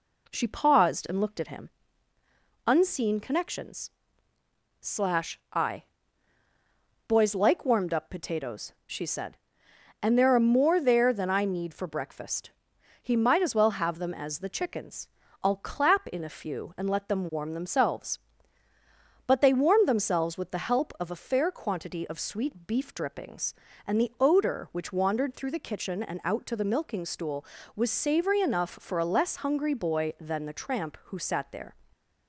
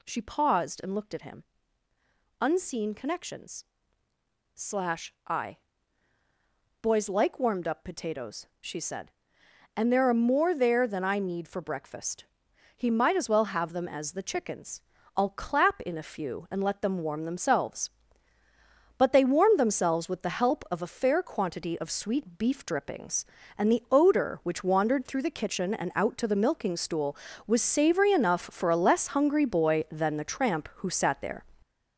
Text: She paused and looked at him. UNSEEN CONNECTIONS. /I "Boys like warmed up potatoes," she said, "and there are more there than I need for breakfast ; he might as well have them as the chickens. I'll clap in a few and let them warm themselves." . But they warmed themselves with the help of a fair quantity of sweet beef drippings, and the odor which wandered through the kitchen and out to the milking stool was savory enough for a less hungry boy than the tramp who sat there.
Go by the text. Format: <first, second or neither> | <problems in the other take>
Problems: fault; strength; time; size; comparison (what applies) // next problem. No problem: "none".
first | gets louder; throughout; 6.5 dB // pauses between "I" and "Boys"; at 5.5 s; 1.2 s long; also in the first